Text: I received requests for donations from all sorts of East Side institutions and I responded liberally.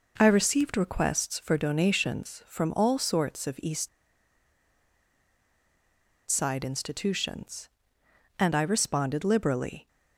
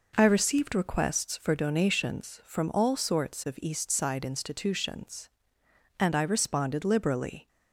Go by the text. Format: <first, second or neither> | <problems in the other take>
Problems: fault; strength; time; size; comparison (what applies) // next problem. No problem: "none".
second | pauses between "East" and "Side"; strong; at 3.8 s; 2.4 s long